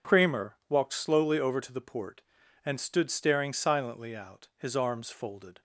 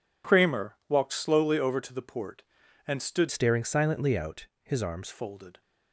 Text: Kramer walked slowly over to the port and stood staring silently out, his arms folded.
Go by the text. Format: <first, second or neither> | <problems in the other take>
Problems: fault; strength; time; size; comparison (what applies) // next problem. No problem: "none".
first | changes voice from "staring" to "arms"; from 3.2 to 5.0 s; 1.8 s long